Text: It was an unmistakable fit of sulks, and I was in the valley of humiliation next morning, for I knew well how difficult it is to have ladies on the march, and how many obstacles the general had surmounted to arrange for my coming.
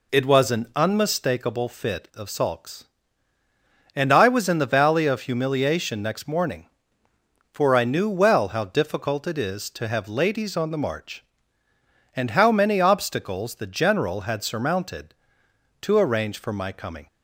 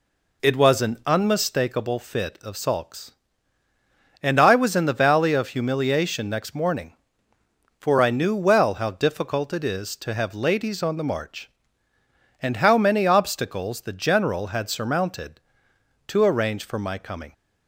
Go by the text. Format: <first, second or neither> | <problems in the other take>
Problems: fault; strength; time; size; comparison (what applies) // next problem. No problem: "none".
neither | none